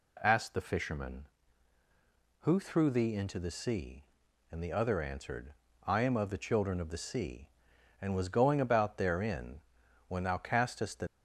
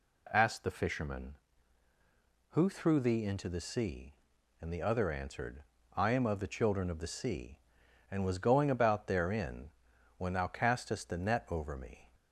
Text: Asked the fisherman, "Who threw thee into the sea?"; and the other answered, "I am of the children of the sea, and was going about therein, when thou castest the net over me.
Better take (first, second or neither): second